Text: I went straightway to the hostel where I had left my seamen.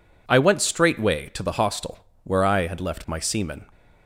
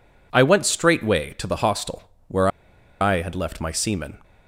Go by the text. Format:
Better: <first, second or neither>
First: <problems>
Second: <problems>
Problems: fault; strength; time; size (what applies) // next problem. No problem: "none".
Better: first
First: pauses between "hostel" and "where"; slight; at 1.9 s; 0.24 s long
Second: pauses between "hostel" and "where"; slight; at 2.0 s; 0.24 s long // pauses between "where" and "I"; noticeable; at 2.4 s; 0.52 s long